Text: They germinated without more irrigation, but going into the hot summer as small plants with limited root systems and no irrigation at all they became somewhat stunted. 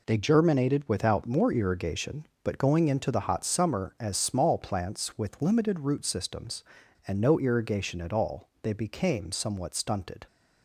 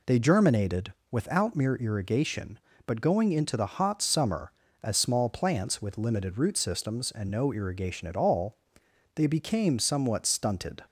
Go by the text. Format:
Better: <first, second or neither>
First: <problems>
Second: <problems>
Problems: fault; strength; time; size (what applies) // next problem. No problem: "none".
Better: first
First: none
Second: pauses between "germinated" and "without"; slight; at 0.9 s; 0.18 s long // says "mere" for "more"; at 1.5 s // pauses between "all" and "they"; noticeable; at 8.5 s; 0.60 s long